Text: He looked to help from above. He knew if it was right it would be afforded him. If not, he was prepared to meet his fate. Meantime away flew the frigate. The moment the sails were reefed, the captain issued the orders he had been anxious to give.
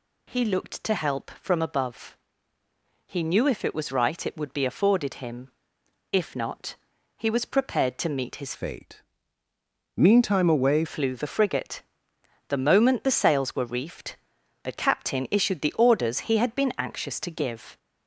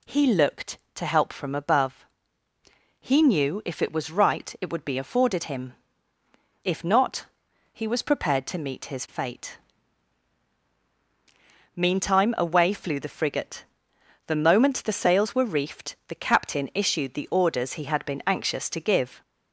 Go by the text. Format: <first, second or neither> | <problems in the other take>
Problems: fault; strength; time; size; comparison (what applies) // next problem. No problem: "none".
second | changes voice from "fate" to "away"; from 8.5 to 10.8 s; 2.3 s long